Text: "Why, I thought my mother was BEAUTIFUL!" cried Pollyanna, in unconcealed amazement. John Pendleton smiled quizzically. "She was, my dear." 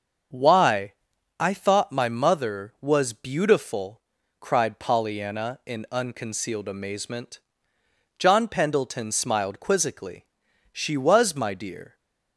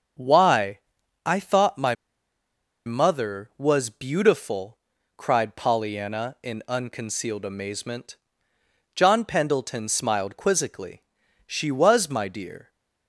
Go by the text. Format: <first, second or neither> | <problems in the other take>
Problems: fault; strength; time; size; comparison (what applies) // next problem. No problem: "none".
first | starts louder than the rest; until 1.6 s; 6.5 dB; also in the first // pauses between "my" and "mother"; noticeable; at 1.9 s; 0.92 s long